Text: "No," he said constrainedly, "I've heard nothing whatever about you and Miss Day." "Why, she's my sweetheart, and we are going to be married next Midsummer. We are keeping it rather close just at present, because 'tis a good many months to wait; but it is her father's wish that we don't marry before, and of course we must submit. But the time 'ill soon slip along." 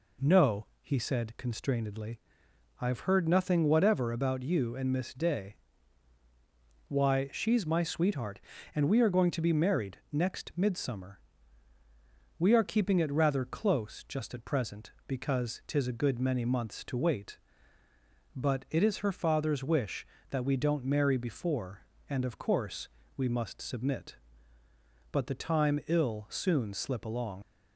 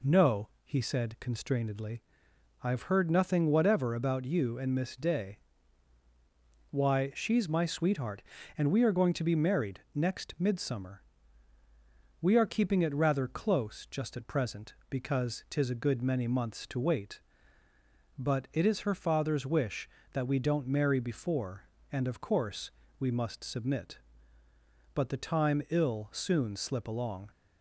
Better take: second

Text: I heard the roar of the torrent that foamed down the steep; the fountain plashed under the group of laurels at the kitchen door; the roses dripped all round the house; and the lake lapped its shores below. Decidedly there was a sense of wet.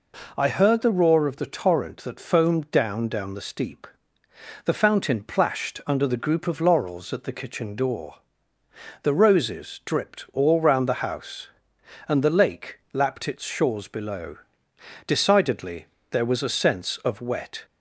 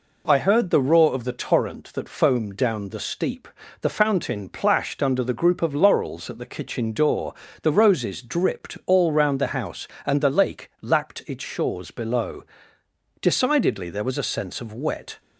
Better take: second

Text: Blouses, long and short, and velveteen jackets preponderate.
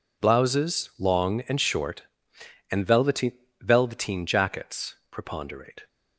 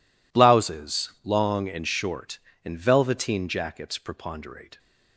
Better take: second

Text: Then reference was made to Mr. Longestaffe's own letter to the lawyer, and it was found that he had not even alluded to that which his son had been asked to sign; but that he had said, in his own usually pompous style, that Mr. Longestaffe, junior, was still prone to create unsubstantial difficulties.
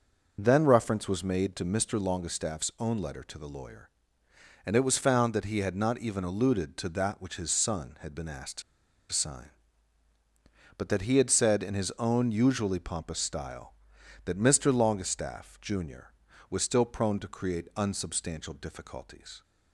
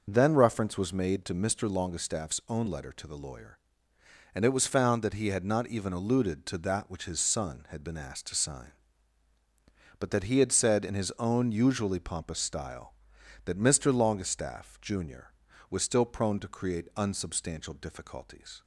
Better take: second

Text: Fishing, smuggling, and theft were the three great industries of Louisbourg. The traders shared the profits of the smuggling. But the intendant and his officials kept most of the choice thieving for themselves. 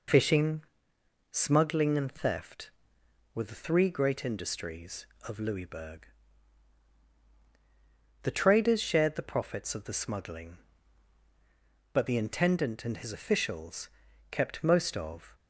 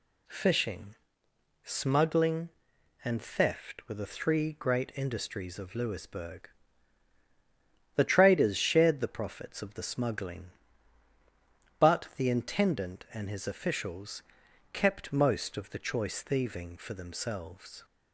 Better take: second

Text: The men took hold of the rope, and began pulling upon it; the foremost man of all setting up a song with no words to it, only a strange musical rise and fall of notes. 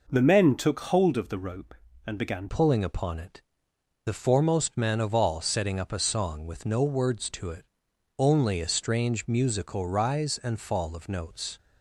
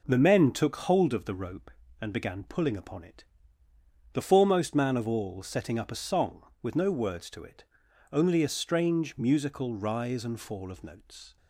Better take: second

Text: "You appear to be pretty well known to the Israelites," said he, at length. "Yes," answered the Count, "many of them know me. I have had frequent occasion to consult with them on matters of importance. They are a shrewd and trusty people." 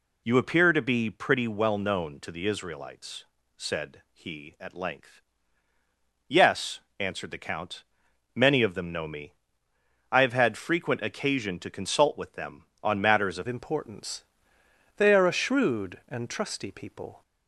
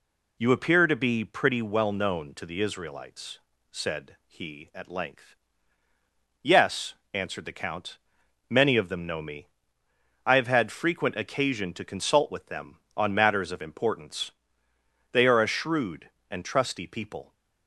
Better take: second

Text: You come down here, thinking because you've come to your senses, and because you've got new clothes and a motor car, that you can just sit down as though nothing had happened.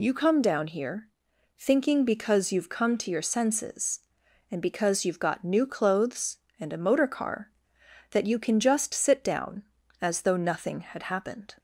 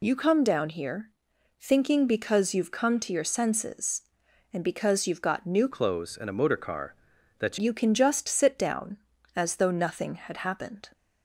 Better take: first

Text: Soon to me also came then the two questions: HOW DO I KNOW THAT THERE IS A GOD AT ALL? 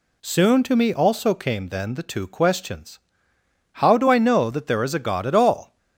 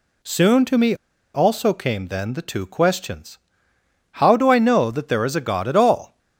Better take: first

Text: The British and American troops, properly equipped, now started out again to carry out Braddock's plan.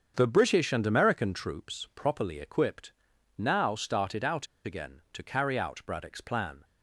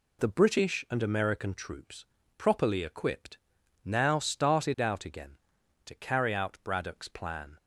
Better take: second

